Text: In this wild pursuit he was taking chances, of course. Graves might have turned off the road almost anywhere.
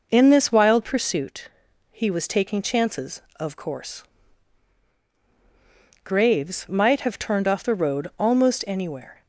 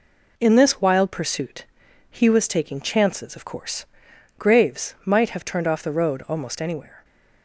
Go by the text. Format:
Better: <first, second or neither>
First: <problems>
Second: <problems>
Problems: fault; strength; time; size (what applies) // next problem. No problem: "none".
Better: neither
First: pauses between "pursuit" and "he"; at 1.4 s; 0.42 s long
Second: pauses between "pursuit" and "he"; noticeable; at 1.6 s; 0.46 s long